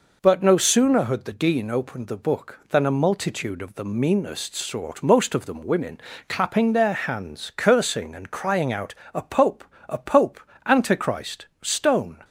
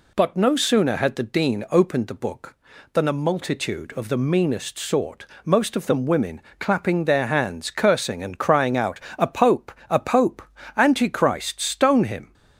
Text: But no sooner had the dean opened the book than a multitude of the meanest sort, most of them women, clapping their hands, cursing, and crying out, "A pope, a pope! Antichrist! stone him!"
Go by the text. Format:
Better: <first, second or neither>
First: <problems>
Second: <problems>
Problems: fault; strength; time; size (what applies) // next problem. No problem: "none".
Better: second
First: stops before "him"; at 12.2 s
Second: none